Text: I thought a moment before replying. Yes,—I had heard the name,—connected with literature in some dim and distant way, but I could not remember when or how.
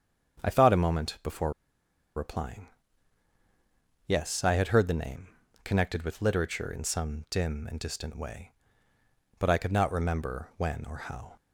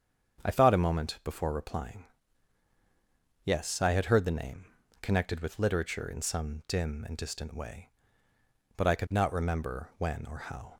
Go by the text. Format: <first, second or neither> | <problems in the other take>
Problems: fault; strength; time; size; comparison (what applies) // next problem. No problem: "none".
second | starts louder than the rest; strong; until 1.4 s; 7.5 dB; strong in the second // pauses between "before" and "replying"; noticeable; at 1.5 s; 0.65 s long